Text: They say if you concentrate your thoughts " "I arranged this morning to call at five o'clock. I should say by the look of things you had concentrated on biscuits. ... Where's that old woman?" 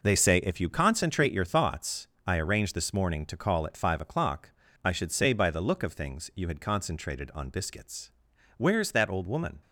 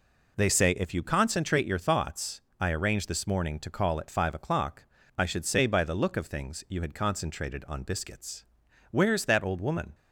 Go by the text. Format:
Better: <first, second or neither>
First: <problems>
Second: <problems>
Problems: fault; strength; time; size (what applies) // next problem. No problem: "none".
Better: second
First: gets quieter; strong; throughout; 8 dB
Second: none